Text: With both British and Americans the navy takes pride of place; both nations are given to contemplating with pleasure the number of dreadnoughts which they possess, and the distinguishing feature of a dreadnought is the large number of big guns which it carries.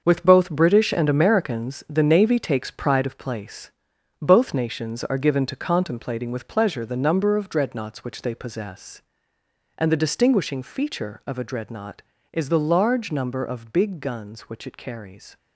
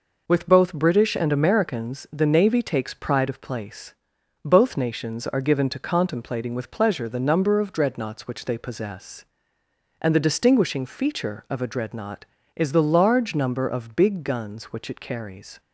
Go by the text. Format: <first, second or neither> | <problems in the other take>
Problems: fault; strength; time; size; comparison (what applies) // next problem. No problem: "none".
second | gets quieter; strong; throughout; 9.5 dB